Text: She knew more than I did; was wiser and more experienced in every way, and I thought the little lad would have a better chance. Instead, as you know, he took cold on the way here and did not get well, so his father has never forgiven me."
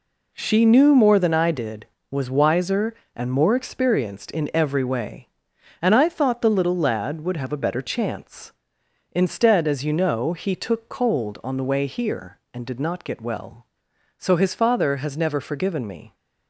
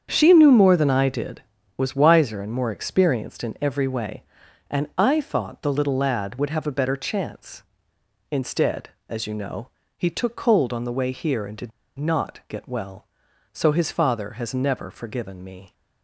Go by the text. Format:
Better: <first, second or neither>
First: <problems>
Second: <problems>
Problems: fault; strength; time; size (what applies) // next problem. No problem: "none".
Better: first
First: none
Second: starts louder than the rest; strong; until 1.1 s; 7.5 dB // pauses between "did" and "not"; slight; at 11.7 s; 0.25 s long